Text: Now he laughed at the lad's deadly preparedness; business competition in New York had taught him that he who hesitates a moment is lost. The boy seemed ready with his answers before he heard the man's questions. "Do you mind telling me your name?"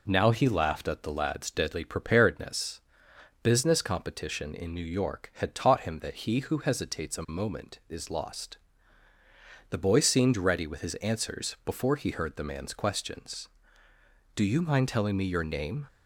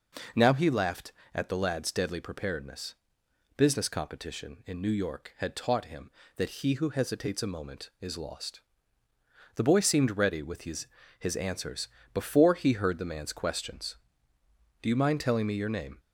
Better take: first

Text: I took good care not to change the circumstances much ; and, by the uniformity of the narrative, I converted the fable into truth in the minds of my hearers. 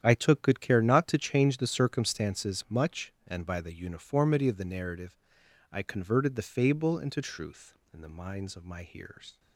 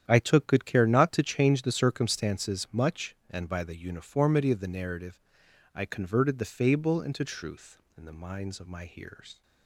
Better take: neither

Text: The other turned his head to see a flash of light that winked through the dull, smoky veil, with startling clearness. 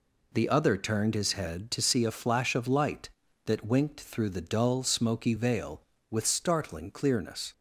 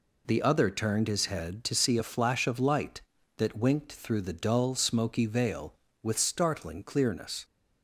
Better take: neither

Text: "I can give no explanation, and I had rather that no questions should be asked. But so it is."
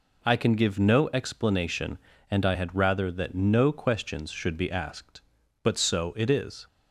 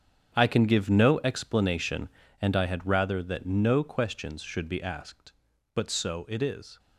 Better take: first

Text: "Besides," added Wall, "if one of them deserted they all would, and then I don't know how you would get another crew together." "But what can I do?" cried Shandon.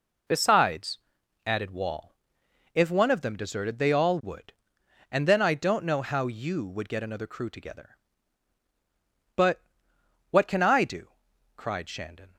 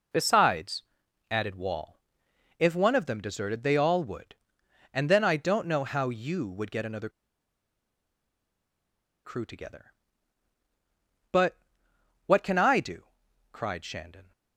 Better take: first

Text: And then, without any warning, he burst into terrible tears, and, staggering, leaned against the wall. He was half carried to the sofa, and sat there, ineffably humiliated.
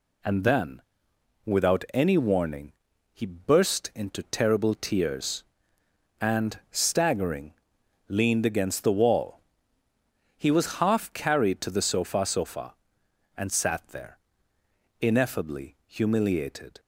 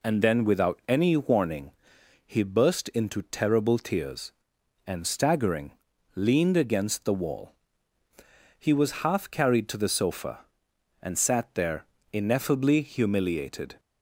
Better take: second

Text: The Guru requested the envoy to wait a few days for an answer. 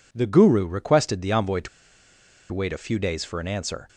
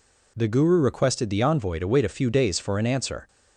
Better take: second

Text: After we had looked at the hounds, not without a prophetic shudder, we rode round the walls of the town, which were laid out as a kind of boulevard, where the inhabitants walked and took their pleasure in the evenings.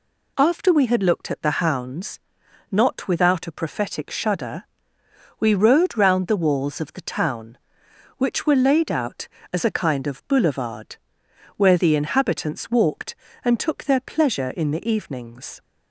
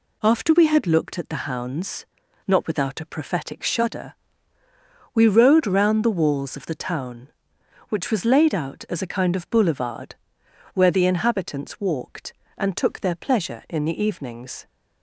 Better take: first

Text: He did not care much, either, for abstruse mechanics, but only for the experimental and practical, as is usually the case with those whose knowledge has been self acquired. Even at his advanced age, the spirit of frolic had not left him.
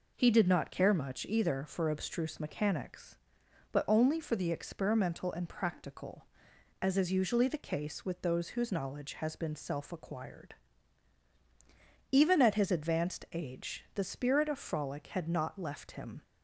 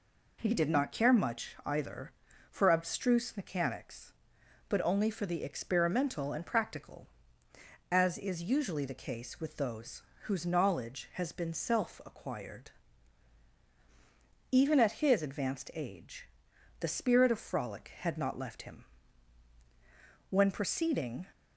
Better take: first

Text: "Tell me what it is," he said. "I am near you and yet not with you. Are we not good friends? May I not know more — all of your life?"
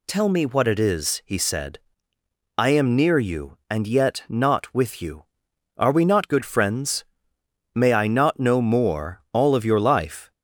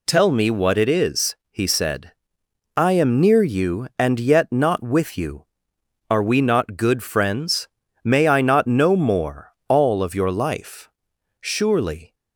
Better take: first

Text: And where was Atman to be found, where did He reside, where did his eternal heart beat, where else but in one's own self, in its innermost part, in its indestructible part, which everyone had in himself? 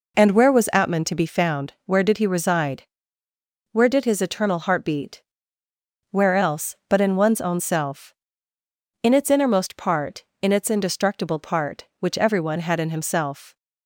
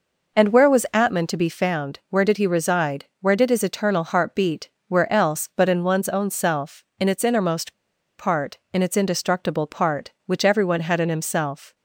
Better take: first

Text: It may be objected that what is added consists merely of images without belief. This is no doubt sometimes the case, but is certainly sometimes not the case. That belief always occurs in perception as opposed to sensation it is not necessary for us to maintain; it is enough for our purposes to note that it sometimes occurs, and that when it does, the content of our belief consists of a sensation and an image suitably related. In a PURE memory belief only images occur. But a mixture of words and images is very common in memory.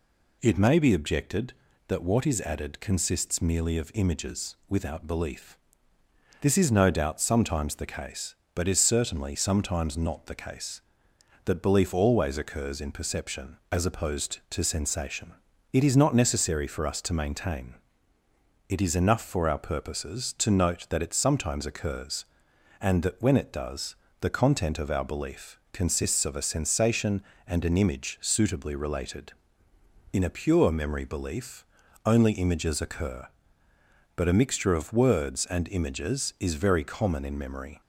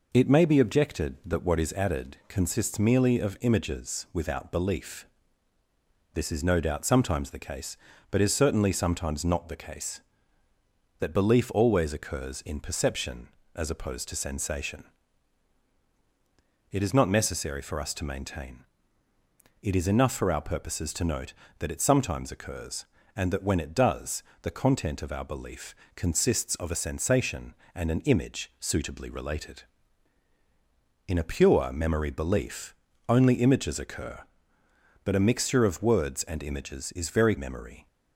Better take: first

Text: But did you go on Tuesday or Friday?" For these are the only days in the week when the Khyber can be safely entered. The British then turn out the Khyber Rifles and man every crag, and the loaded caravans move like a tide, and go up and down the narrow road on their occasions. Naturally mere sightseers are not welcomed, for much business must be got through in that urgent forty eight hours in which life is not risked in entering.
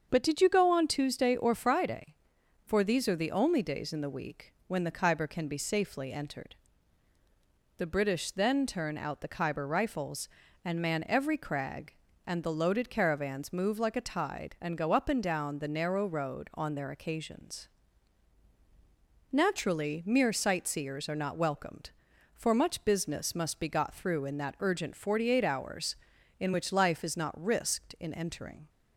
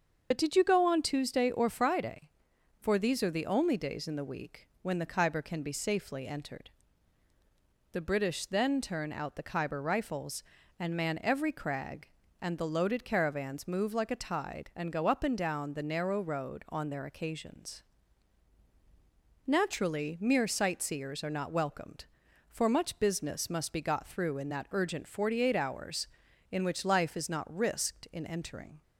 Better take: first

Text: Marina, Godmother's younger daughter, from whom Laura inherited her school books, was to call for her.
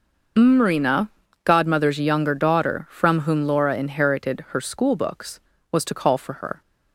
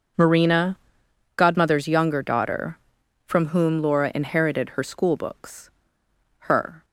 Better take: first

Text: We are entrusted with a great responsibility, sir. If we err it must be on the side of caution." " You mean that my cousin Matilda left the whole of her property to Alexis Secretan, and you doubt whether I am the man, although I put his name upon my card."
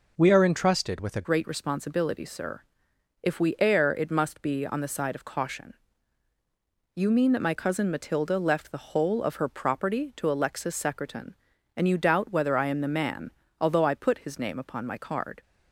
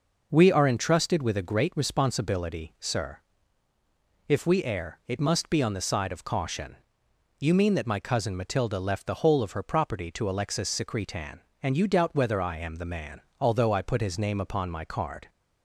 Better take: second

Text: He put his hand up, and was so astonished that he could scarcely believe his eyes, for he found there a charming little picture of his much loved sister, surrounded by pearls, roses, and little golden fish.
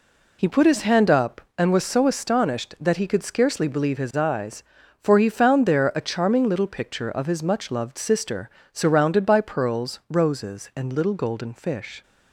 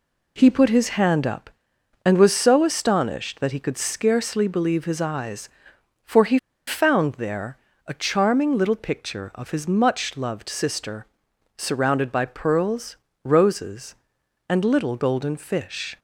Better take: first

